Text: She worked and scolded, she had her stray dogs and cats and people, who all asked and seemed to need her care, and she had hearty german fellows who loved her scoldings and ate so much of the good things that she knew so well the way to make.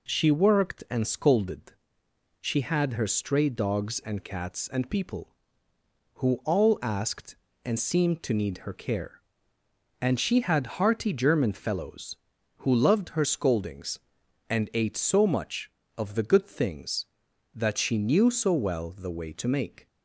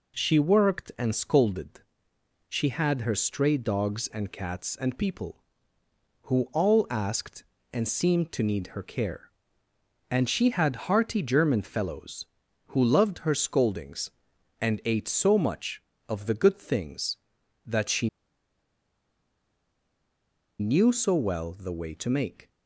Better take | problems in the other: first | pauses between "she" and "knew"; strong; at 18.0 s; 2.5 s long

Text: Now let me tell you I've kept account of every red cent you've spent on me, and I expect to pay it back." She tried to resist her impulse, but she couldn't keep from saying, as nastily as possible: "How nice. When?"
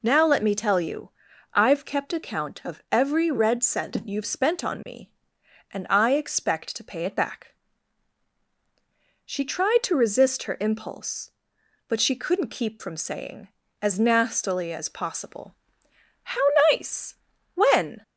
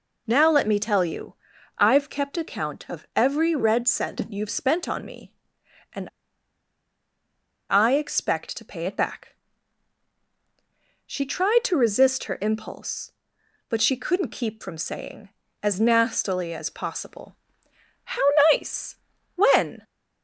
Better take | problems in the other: first | pauses between "you" and "I've"; at 1.3 s; 0.44 s long; also in the first // pauses between "and" and "I"; strong; at 6.0 s; 1.6 s long // pauses between "How" and "nice"; slight; at 18.2 s; 0.26 s long; slight in the first

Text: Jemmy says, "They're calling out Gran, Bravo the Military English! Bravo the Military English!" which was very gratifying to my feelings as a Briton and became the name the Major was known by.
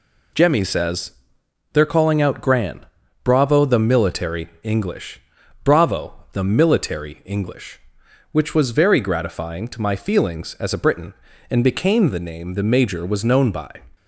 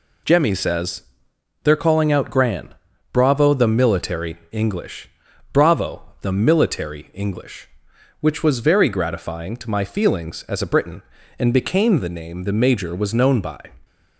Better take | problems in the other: neither | pauses between "Military" and "English"; slight; the same in both // pauses between "Bravo" and "the"; slight; the same in both

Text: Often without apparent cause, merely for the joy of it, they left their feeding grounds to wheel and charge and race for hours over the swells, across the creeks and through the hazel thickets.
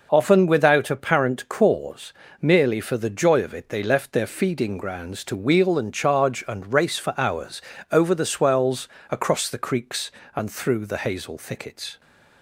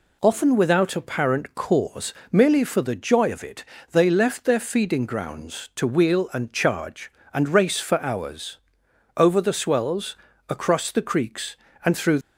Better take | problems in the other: first | pauses between "hours" and "over"; noticeable; at 8.5 s; 0.58 s long; slight in the first // stops before "the hazel thickets"; at 12.2 s

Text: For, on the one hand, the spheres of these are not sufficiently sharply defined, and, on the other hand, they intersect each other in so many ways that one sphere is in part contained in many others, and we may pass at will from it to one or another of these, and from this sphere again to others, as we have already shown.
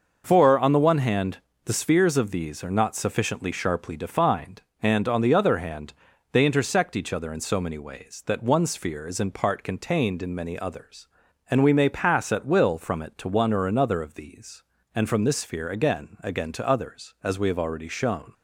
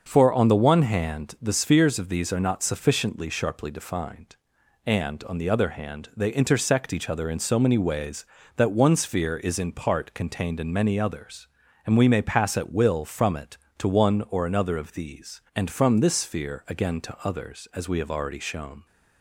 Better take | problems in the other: second | starts louder than the rest; noticeable; until 1.2 s; 6 dB; also in the second // says "again" twice; at 16.2 s

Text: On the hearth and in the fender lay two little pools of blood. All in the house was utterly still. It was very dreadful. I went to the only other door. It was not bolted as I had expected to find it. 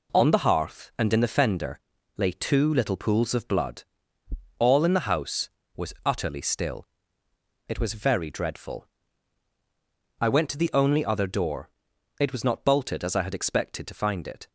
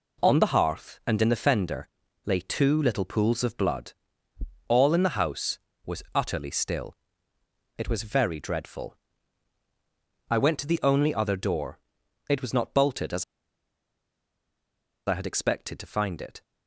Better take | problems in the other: first | pauses between "fender" and "lay"; at 1.8 s; 0.38 s long; also in the first // pauses between "as" and "I"; strong; at 13.2 s; 1.8 s long

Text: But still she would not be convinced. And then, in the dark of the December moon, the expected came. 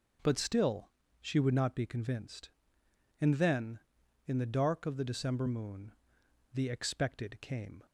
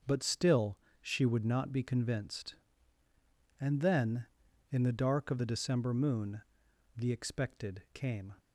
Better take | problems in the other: neither | starts louder than the rest; the same in both // pauses between "still" and "she"; slight; the same in both

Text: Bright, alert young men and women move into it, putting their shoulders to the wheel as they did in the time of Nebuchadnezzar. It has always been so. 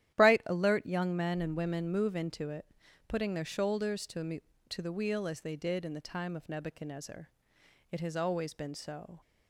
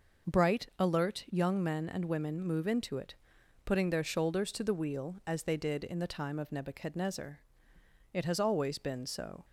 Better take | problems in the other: second | starts louder than the rest; strong; until 1.1 s; 11.5 dB // says "to" twice; at 4.6 s

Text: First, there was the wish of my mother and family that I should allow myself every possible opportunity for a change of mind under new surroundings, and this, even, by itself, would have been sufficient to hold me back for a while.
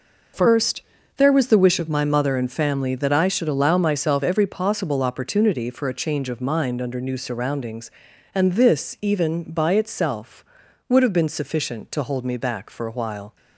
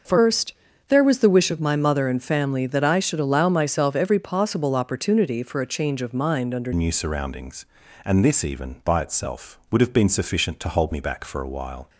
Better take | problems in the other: first | starts louder than the rest; noticeable; until 1.3 s; 6 dB // changes voice at "new"; from 6.7 s on; 5.1 s long

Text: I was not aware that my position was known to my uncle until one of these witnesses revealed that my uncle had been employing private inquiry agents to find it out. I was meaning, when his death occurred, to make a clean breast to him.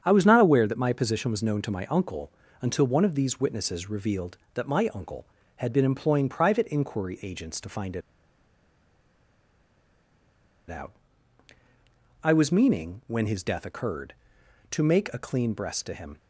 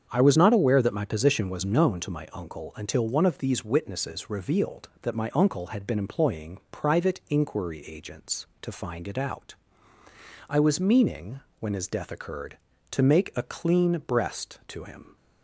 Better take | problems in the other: second | starts louder than the rest; strong; until 1.0 s; 7.5 dB; strong in the second // pauses between "uncle" and "until"; slight; at 2.3 s; 0.28 s long // pauses between "it" and "out"; strong; at 8.0 s; 2.6 s long

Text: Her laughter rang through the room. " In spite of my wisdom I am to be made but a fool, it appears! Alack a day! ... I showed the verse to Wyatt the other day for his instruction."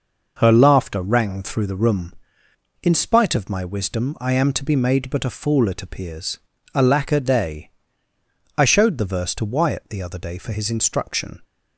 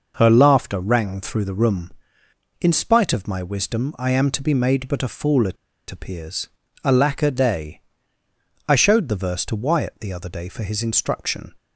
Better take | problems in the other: first | pauses between "it" and "appears"; slight; at 5.5 s; 0.34 s long

